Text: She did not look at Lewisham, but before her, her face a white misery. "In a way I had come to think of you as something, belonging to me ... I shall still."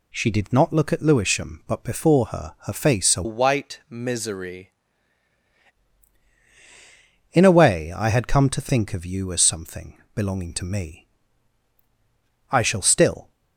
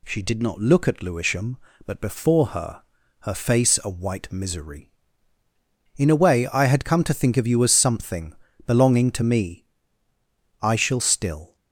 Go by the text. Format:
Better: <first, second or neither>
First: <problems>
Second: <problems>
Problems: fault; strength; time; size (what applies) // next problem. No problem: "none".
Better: second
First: changes voice from "white" to "misery"; from 3.2 to 4.7 s; 1.5 s long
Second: none